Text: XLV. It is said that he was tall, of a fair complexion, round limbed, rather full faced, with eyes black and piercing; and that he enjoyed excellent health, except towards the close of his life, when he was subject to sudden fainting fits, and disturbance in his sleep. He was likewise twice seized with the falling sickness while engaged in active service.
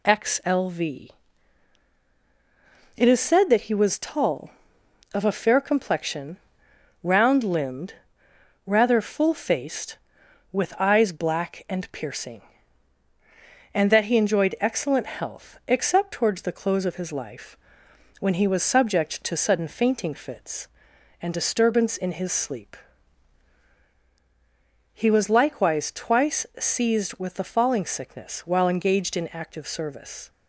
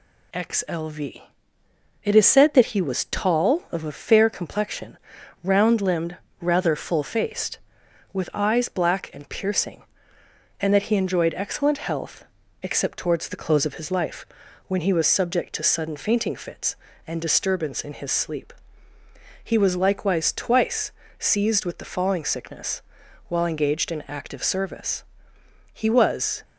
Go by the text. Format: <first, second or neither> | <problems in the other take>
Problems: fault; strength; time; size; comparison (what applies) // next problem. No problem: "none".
first | pauses between "twice" and "seized"; slight; at 20.9 s; 0.26 s long // pauses between "sickness" and "while"; noticeable; at 22.8 s; 0.48 s long // goes on to say "He was"; noticeable; from 25.7 s on; 0.70 s long